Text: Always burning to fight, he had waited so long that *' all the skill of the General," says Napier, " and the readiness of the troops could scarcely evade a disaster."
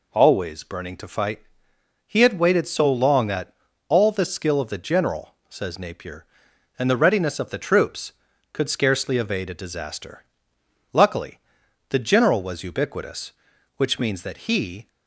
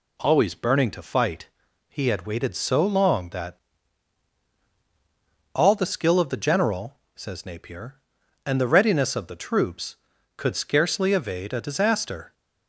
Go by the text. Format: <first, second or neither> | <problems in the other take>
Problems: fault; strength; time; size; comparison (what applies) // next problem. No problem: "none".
second | goes on to say "Luckily the General was ubiquitous which means that he"; strong; from 10.9 s on; 3.9 s long